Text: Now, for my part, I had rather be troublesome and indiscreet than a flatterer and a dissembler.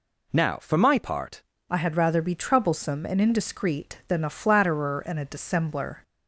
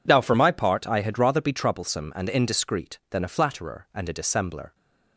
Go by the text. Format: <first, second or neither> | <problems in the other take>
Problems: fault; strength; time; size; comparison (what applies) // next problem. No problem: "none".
second | changes voice at "I"; from 1.6 s on; 4.4 s long